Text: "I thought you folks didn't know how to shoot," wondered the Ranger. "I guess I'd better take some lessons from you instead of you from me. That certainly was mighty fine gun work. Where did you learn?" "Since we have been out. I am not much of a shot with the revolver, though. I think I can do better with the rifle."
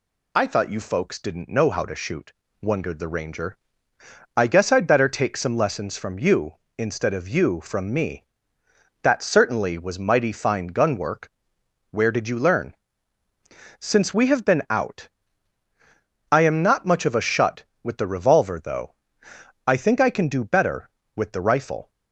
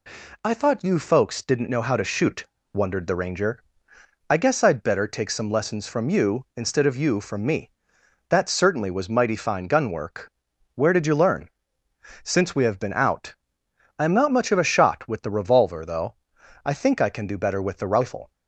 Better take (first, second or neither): second